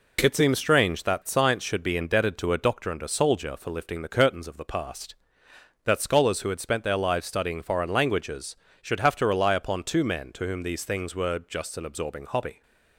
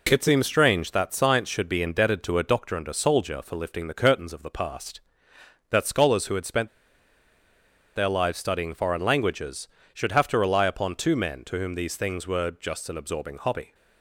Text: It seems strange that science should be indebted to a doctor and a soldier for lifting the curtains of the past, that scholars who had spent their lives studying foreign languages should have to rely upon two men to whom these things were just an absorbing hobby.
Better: first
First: none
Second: pauses between "spent" and "their"; strong; at 6.6 s; 1.2 s long

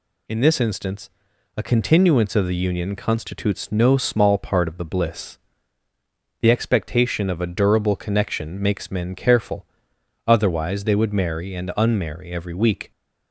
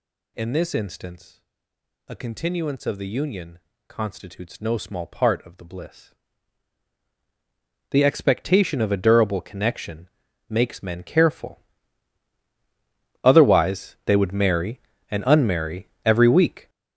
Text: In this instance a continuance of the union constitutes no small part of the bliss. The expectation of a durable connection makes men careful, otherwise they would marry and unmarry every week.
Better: first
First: pauses between "instance" and "a"; noticeable; at 1.1 s; 0.46 s long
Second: gets louder; strong; throughout; 10.5 dB // pauses between "instance" and "a"; noticeable; at 1.4 s; 0.66 s long // pauses between "union" and "constitutes"; slight; at 3.5 s; 0.28 s long // pauses between "connection" and "makes"; at 10.0 s; 0.38 s long // pauses between "unmarry" and "every"; slight; at 15.8 s; 0.18 s long

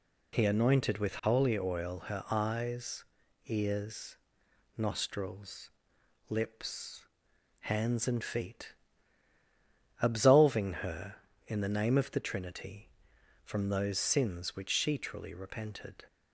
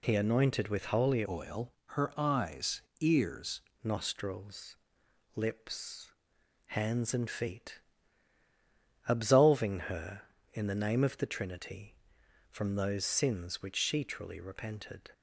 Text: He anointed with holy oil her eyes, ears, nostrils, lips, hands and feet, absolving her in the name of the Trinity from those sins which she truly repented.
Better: first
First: none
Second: changes voice from "oil" to "ears"; from 1.2 to 3.5 s; 2.3 s long

